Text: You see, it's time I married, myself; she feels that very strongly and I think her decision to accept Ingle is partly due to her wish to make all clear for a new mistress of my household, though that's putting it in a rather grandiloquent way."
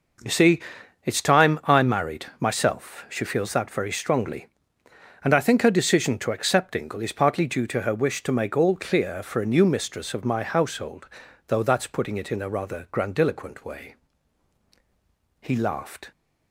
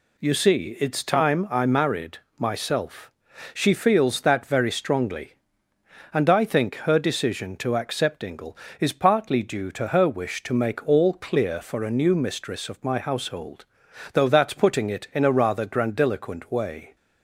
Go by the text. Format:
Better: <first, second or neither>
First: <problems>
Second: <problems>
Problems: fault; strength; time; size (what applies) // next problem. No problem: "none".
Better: second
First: goes on to say "He laughed"; noticeable; from 15.4 s on; 0.70 s long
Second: none